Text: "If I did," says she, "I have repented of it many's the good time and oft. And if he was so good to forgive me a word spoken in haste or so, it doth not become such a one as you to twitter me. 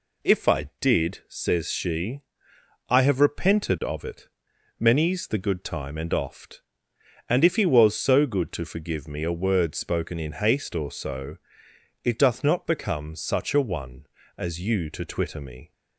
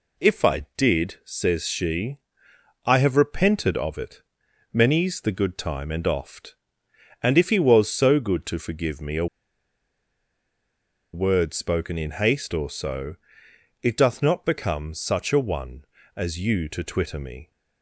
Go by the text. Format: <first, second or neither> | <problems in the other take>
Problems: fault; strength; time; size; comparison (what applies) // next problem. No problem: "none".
first | pauses between "it" and "many's"; noticeable; at 4.2 s; 0.50 s long; noticeable in the first // pauses between "a" and "word"; strong; at 9.2 s; 1.8 s long